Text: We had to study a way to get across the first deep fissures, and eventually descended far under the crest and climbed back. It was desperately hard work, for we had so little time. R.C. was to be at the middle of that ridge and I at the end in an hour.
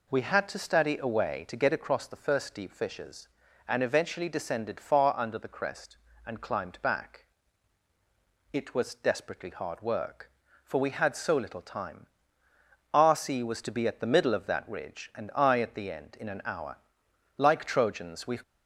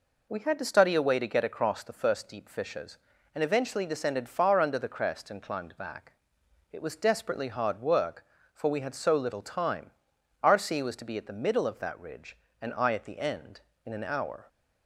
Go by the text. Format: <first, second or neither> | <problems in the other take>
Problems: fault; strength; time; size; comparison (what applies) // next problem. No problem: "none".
second | goes on to say "Like Trojans we"; noticeable; from 17.3 s on; 1.0 s long